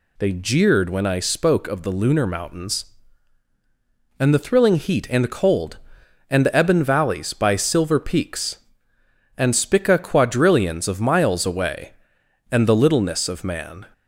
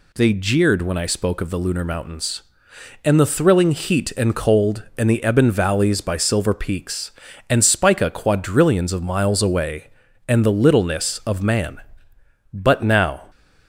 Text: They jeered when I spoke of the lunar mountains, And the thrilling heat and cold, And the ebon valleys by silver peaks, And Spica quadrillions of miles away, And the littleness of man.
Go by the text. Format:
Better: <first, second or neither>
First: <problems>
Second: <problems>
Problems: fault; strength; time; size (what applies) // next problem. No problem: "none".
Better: first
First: none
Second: goes on to say "But now"; noticeable; from 12.5 s on; 0.78 s long